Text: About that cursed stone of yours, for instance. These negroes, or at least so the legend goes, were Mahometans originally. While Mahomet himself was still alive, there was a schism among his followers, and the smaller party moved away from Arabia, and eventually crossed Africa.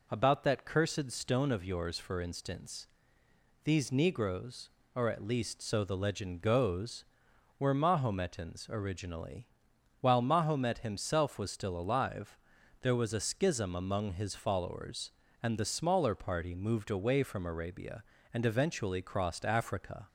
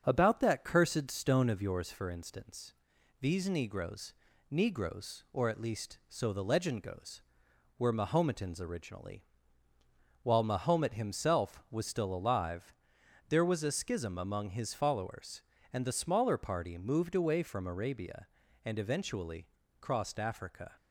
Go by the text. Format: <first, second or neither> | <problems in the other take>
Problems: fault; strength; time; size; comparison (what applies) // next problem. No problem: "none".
first | starts louder than the rest; strong; until 1.0 s; 7 dB // says "negroes" twice; at 4.5 s // pauses between "eventually" and "crossed"; slight; at 19.4 s; 0.34 s long